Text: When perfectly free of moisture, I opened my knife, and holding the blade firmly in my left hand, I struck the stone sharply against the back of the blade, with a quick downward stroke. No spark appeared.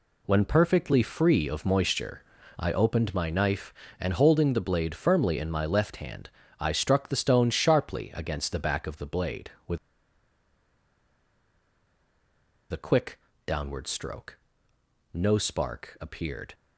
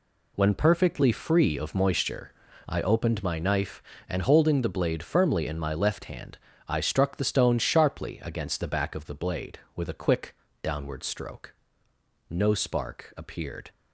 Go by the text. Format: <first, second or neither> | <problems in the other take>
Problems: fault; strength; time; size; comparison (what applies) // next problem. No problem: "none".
second | pauses between "with" and "a"; strong; at 9.7 s; 2.9 s long // pauses between "quick" and "downward"; slight; at 13.1 s; 0.28 s long; slight in the second